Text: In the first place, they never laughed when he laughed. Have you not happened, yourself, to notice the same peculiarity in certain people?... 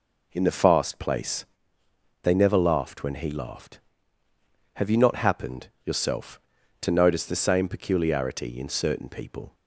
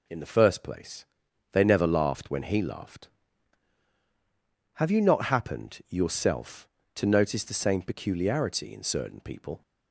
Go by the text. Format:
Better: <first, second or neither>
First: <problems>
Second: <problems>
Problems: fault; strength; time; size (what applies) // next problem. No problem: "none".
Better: second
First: says "fast" for "first"; at 0.5 s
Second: none